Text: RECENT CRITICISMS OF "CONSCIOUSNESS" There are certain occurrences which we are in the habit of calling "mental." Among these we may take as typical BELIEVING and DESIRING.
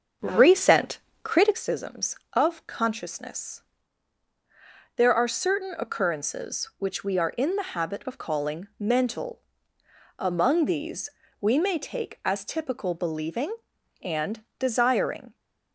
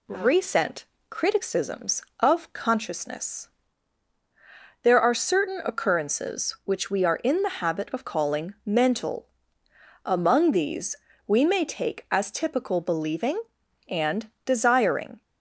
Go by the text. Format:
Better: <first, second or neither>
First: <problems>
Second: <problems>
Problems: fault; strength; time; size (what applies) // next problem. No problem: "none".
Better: second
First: starts louder than the rest; until 1.6 s; 7 dB // pauses between "RECENT" and "CRITICISMS"; slight; at 0.9 s; 0.26 s long // pauses between "CONSCIOUSNESS" and "There"; strong; at 3.6 s; 1.3 s long // pauses between "these" and "we"; slight; at 11.1 s; 0.28 s long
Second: pauses between "RECENT" and "CRITICISMS"; slight; at 0.8 s; 0.26 s long // pauses between "CONSCIOUSNESS" and "There"; strong; at 3.4 s; 1.3 s long // pauses between "these" and "we"; slight; at 10.9 s; 0.28 s long